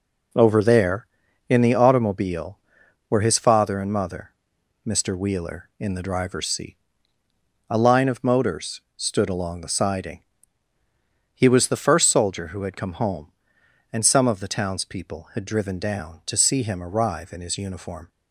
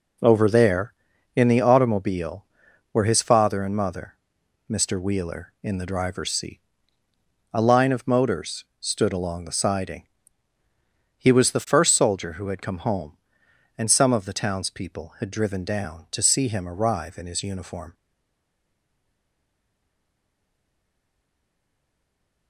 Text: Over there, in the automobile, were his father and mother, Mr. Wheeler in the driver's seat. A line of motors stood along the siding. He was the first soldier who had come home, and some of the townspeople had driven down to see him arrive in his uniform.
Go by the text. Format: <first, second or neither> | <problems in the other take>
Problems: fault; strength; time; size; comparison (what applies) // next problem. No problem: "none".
first | pauses between "motors" and "stood"; slight; at 8.6 s; 0.16 s long; slight in the first // stays silent after the last word; strong; from 17.9 s on; 4.5 s long